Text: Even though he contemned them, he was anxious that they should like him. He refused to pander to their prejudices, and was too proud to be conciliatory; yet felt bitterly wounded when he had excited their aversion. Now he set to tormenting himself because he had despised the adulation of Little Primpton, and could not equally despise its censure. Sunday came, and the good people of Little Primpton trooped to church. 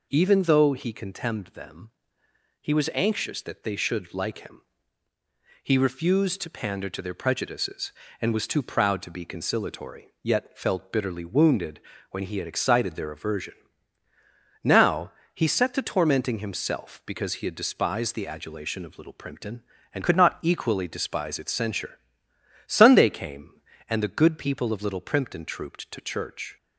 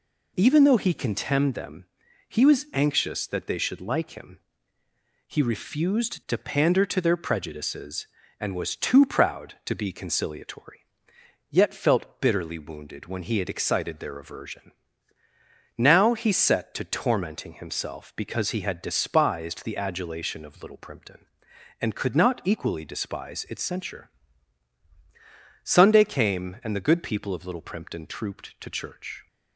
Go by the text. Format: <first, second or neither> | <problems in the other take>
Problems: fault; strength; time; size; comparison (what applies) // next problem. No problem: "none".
second | pauses between "wounded" and "when"; slight; at 11.8 s; 0.32 s long // pauses between "Now" and "he"; slight; at 15.1 s; 0.24 s long // changes voice from "could" to "not"; from 20.0 to 20.3 s; 0.3 s long